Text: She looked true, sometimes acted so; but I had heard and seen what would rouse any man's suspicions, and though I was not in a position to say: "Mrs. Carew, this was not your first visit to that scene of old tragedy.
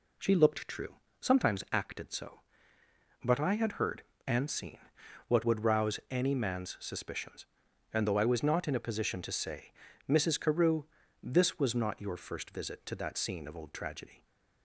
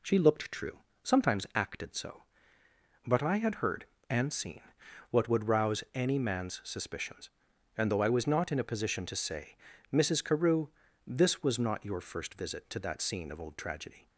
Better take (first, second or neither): neither